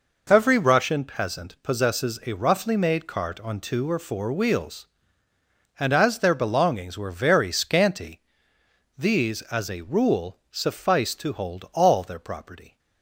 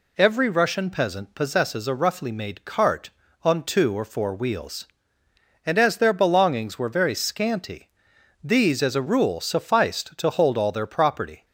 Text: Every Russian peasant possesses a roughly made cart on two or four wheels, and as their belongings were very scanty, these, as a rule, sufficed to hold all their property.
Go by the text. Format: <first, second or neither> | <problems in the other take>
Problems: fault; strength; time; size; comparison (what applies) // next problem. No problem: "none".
neither | none